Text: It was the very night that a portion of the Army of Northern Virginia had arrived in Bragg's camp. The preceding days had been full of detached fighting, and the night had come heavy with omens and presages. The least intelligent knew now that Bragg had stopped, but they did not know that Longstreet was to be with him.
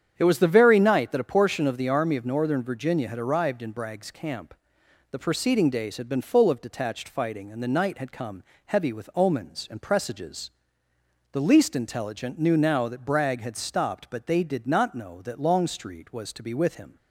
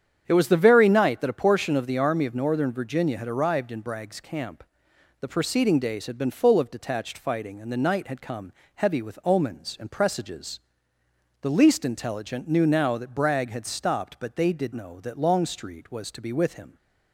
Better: first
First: starts louder than the rest; strong; until 1.1 s; 8.5 dB // pauses between "come" and "heavy"; slight; at 8.4 s; 0.24 s long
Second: starts louder than the rest; strong; until 1.2 s; 8.5 dB // pauses between "come" and "heavy"; slight; at 8.5 s; 0.24 s long // skips "not"; at 14.7 s

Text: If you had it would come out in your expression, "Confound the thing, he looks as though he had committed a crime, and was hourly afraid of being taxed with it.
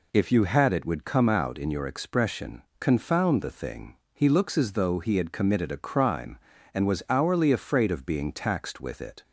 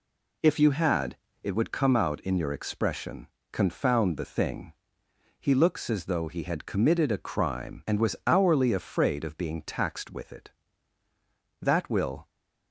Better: first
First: none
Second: pauses between "had" and "it"; slight; at 1.1 s; 0.28 s long // goes on to say "That will"; noticeable; from 11.6 s on; 0.68 s long

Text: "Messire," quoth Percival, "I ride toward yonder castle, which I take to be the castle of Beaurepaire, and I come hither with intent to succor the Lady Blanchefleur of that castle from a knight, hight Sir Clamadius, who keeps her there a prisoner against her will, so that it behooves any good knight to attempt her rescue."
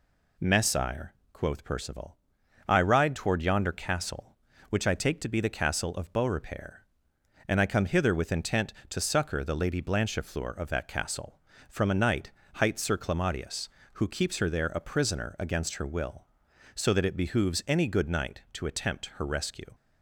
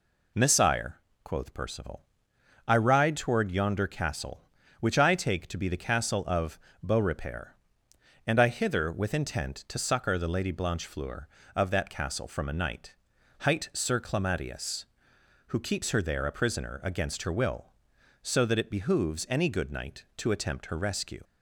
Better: first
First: none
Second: pauses between "of" and "Beaurepaire"; slight; at 6.5 s; 0.24 s long // skips "come"; at 8.4 s

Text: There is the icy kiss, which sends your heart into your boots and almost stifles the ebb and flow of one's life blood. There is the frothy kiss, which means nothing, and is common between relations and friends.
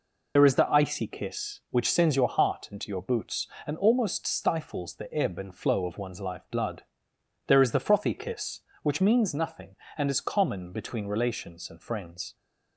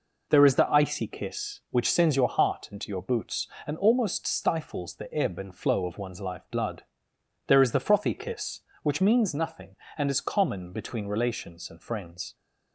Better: second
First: loses the start of "There"; at 0.3 s; 60 ms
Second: none

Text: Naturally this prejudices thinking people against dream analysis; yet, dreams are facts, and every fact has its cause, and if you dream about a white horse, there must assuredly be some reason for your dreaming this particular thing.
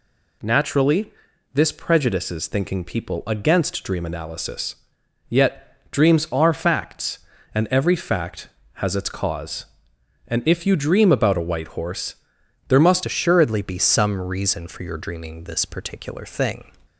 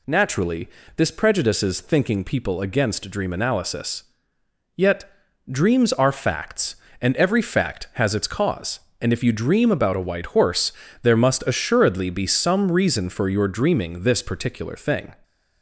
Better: second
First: pauses between "Naturally" and "this"; at 1.1 s; 0.44 s long // changes voice at "assuredly"; from 13.0 s on; 3.7 s long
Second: pauses between "Naturally" and "this"; slight; at 0.6 s; 0.30 s long

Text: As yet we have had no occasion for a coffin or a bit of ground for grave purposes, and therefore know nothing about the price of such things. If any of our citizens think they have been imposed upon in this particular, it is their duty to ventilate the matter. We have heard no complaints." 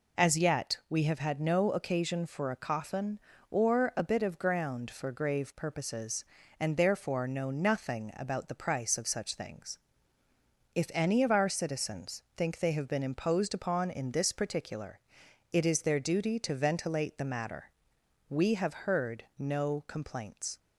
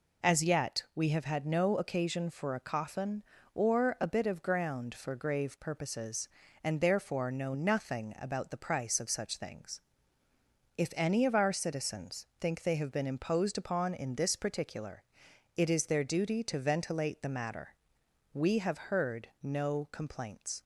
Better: neither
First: pauses between "citizens" and "think"; slight; at 12.2 s; 0.16 s long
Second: pauses between "citizens" and "think"; slight; at 12.2 s; 0.16 s long

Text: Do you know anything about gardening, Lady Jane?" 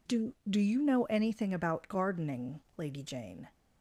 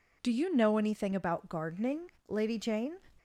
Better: second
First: says "Do" twice; at 0.4 s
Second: none

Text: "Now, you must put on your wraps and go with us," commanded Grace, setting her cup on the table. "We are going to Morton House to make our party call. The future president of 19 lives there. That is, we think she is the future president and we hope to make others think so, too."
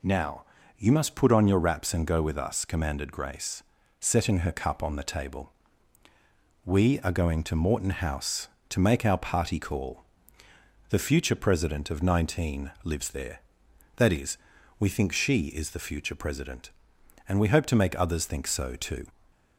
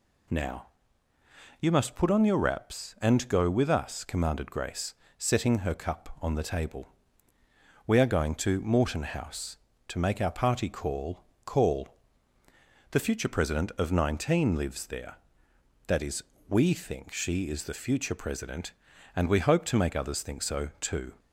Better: first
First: none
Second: says "call" twice; at 11.4 s

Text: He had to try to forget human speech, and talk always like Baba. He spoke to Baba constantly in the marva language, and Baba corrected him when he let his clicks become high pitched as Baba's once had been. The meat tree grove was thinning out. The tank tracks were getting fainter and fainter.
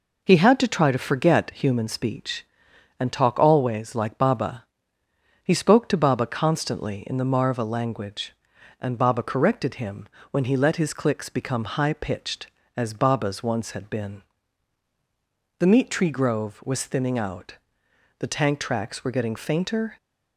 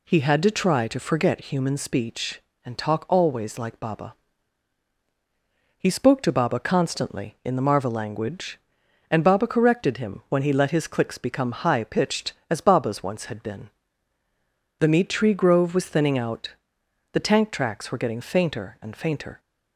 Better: second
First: pauses between "him" and "when"; slight; at 10.0 s; 0.24 s long // stops before "and fainter"; at 19.9 s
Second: none

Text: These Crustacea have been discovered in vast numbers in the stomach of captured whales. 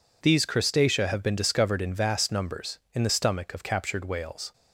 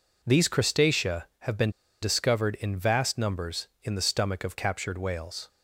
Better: first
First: none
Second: pauses between "been" and "discovered"; slight; at 1.7 s; 0.30 s long

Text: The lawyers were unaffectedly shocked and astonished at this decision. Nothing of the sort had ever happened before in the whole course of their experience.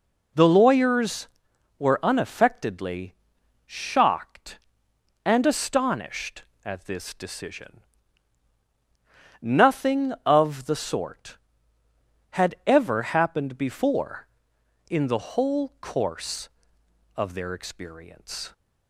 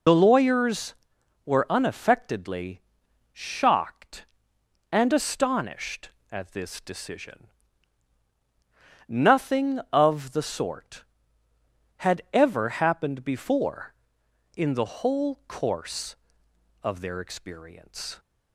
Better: first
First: pauses between "unaffectedly" and "shocked"; noticeable; at 3.1 s; 0.54 s long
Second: loses the start of "The"; at 0.0 s; 50 ms // pauses between "unaffectedly" and "shocked"; noticeable; at 2.7 s; 0.54 s long

